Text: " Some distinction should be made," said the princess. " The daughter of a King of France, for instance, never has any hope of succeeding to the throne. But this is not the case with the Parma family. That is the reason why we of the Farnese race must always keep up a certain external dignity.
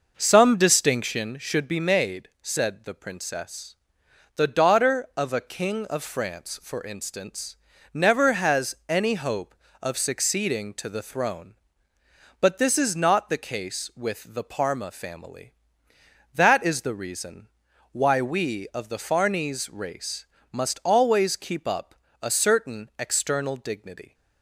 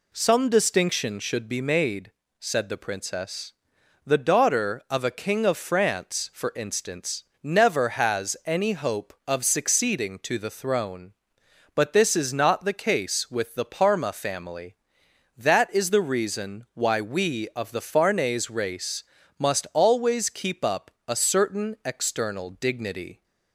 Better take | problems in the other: second | starts louder than the rest; noticeable; until 1.3 s; 5.5 dB // pauses between "reason" and "why"; at 17.4 s; 0.42 s long // pauses between "race" and "must"; slight; at 20.2 s; 0.26 s long; slight in the second // pauses between "up" and "a"; slight; at 21.9 s; 0.28 s long; slight in the second

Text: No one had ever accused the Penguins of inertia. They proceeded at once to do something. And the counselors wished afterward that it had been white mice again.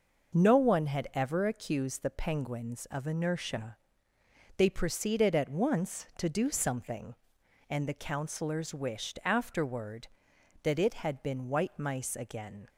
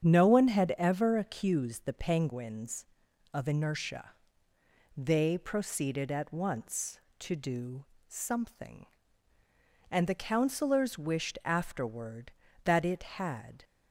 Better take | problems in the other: first | starts louder than the rest; strong; until 1.0 s; 8 dB // pauses between "do" and "something"; slight; at 7.8 s; 0.24 s long // stops before "been white mice again"; at 13.6 s

